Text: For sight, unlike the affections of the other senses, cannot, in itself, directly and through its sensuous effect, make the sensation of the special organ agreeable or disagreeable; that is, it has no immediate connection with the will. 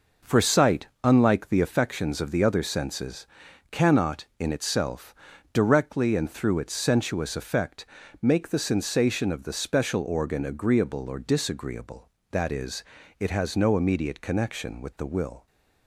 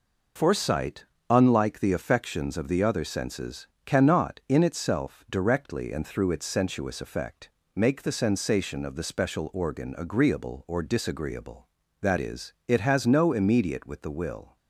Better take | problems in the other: first | skips "connection"; at 13.8 s

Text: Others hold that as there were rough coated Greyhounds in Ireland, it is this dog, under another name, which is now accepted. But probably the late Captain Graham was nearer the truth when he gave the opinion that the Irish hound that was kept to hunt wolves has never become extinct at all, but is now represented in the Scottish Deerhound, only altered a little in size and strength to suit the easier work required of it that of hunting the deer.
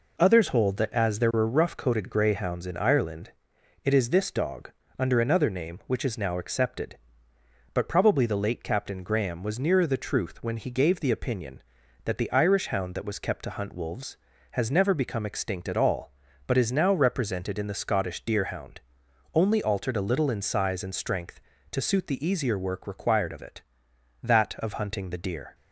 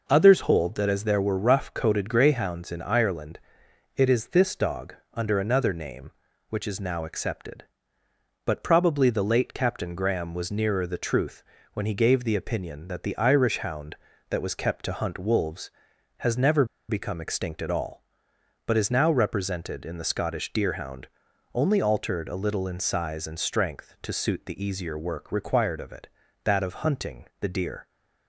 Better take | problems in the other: first | pauses between "truth" and "when"; slight; at 11.4 s; 0.30 s long // pauses between "never" and "become"; slight; at 16.6 s; 0.24 s long

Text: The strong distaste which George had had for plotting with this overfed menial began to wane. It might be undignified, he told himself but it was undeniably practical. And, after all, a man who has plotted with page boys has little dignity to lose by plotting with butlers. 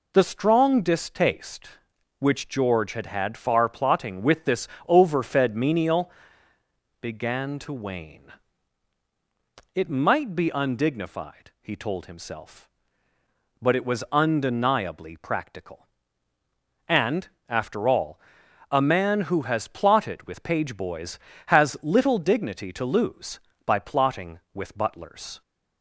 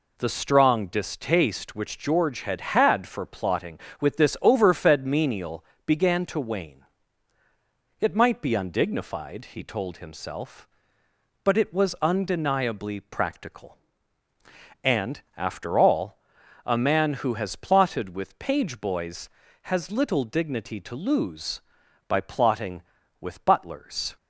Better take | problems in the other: second | says "far" for "for"; at 3.3 s // pauses between "this" and "overfed"; slight; at 4.6 s; 0.20 s long // pauses between "menial" and "began"; noticeable; at 6.1 s; 0.88 s long; slight in the second

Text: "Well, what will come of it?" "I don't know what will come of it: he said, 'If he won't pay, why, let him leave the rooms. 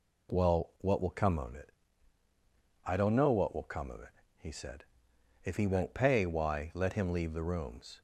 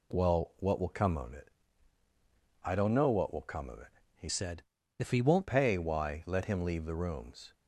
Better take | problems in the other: first | changes voice from "said" to "won't"; from 4.2 to 5.4 s; 1.2 s long

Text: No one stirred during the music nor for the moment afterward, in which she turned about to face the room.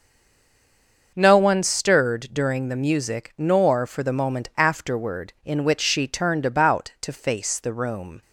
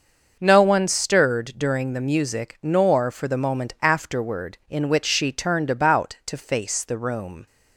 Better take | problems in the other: second | stays silent before the first word; until 1.1 s; 1.1 s long // starts louder than the rest; until 2.1 s; 6.5 dB; also in the second

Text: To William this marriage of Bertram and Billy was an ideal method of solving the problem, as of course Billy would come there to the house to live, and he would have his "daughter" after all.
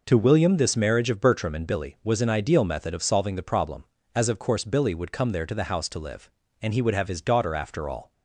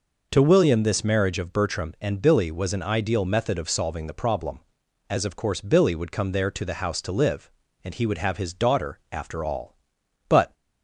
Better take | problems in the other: first | goes on to say "But"; slight; from 10.2 s on; 0.26 s long

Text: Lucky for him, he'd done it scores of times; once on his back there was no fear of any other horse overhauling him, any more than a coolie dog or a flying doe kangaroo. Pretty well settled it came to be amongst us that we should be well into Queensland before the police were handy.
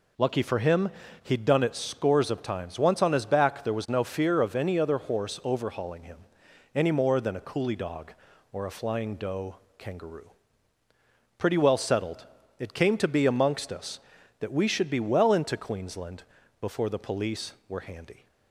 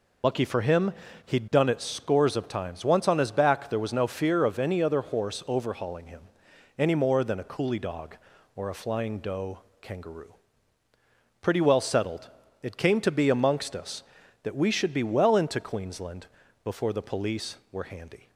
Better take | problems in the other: first | loses the start of "Lucky"; at 0.2 s; 45 ms // pauses between "doe" and "kangaroo"; slight; at 9.6 s; 0.20 s long; slight in the first // pauses between "settled" and "it"; slight; at 12.2 s; 0.32 s long; slight in the first // pauses between "Queensland" and "before"; slight; at 16.2 s; 0.36 s long; slight in the first

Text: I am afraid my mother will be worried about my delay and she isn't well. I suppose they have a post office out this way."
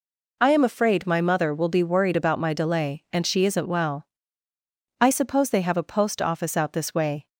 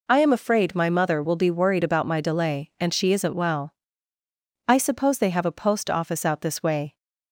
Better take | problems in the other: neither | none

